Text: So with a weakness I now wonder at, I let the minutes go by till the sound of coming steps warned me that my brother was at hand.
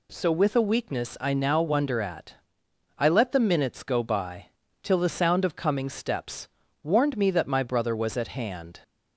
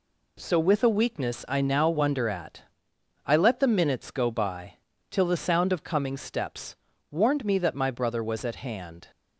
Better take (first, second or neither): first